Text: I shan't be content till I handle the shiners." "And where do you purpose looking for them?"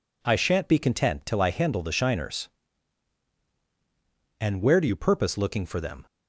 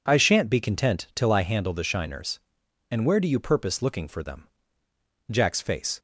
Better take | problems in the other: first | goes on to say "Jack's face"; noticeable; from 5.2 s on; 0.70 s long

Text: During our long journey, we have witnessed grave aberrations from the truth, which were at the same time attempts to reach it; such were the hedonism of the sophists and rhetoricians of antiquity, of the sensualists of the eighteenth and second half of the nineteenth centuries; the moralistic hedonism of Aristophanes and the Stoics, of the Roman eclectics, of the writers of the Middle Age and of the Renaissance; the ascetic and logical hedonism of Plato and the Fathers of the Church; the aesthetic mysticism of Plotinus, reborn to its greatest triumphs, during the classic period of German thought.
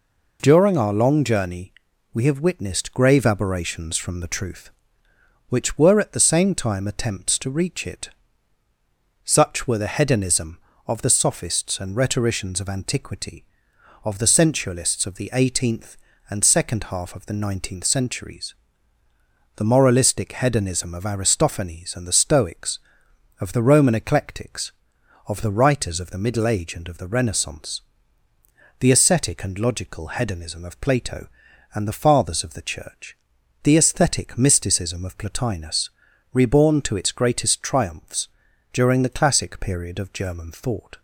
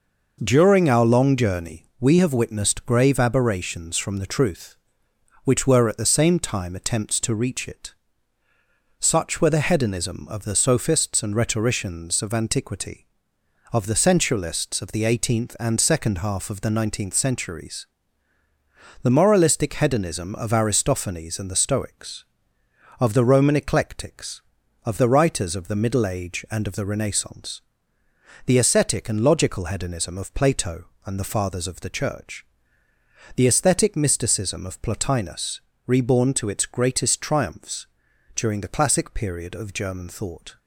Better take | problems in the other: neither | none

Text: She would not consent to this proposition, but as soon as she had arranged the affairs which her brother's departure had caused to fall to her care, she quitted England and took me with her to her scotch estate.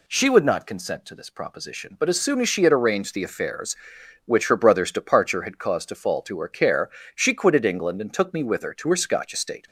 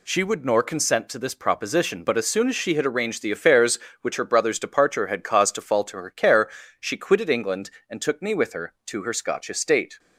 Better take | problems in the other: first | says "nor" for "not"; at 0.4 s

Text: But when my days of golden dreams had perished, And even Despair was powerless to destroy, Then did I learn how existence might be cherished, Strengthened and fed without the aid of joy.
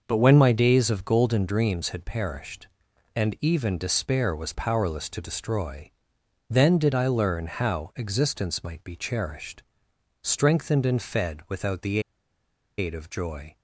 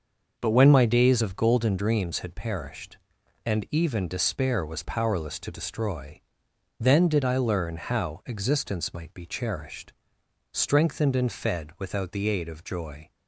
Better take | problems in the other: second | starts louder than the rest; noticeable; until 1.0 s; 6 dB // pauses between "the" and "aid"; noticeable; at 11.9 s; 0.78 s long

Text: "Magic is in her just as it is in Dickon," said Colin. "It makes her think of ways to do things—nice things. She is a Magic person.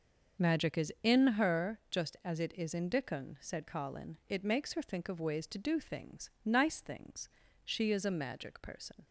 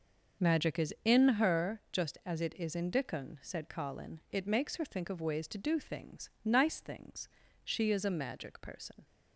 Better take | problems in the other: neither | starts louder than the rest; the same in both

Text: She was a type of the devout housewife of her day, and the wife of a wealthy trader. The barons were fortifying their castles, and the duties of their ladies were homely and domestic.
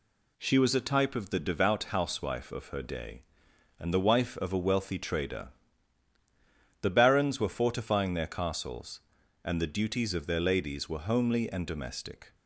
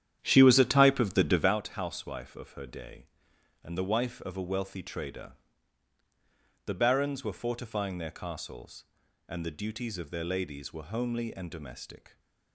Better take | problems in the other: first | starts louder than the rest; strong; until 1.6 s; 10 dB

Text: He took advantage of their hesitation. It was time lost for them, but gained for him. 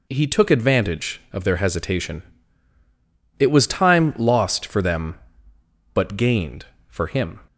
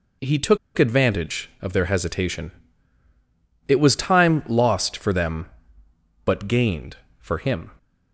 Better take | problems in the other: first | pauses between "took" and "advantage"; slight; at 0.5 s; 0.19 s long

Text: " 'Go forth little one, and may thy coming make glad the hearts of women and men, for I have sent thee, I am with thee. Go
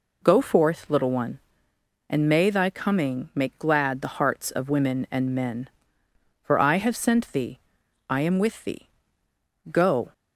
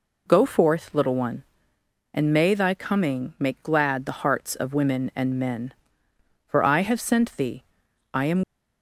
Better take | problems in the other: first | stops before "with thee Go"; at 8.4 s

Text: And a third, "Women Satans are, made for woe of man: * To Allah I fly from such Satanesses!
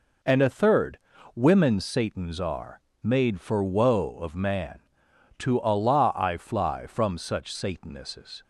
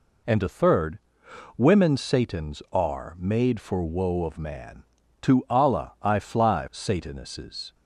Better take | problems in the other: first | skips "from such"; at 6.6 s

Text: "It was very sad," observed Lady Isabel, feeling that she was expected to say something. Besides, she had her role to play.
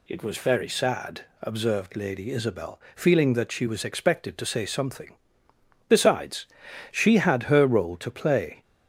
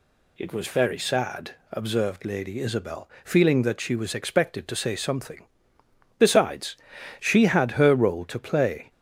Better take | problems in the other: neither | none

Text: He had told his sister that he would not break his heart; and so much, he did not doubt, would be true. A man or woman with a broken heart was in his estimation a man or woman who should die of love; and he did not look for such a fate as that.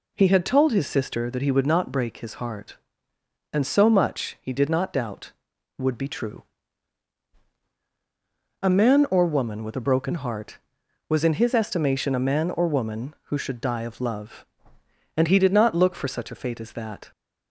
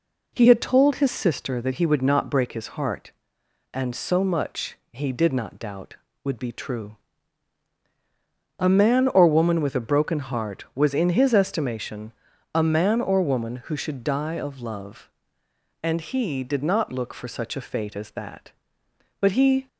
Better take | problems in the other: first | pauses between "estimation" and "a"; at 12.1 s; 0.44 s long // goes on to say "But he"; slight; from 19.1 s on; 0.48 s long

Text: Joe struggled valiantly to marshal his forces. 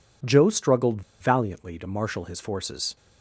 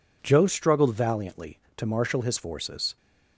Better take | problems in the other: second | pauses between "struggled" and "valiantly"; slight; at 1.0 s; 0.19 s long

